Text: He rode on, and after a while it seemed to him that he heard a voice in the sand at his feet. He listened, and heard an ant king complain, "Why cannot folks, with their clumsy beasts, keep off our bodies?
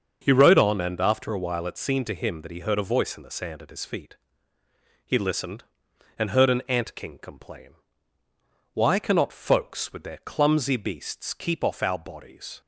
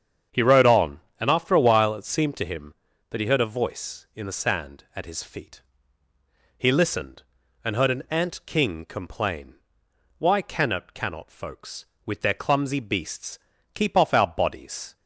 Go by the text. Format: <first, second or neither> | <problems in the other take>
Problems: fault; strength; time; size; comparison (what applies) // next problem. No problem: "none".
first | starts louder than the rest; strong; until 1.5 s; 7.5 dB; also in the first // says "cannot" twice; at 10.9 s